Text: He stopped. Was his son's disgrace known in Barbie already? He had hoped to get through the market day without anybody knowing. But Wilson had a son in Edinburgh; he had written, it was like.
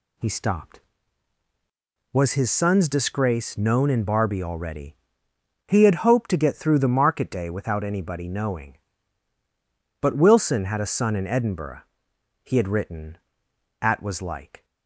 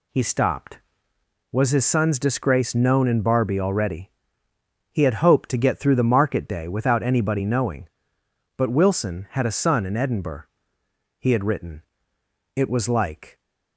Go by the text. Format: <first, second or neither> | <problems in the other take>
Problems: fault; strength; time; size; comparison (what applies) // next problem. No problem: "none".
second | says "at" for "it"; at 13.8 s